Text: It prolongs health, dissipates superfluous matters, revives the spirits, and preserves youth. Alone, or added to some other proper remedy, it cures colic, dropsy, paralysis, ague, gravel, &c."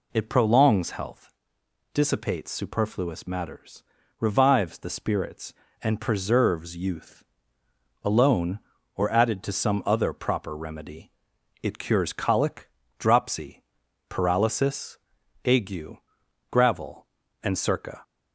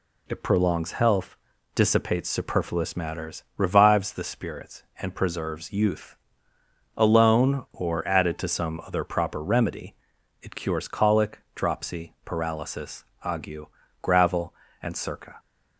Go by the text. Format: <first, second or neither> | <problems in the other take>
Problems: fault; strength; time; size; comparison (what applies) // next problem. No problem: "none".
neither | none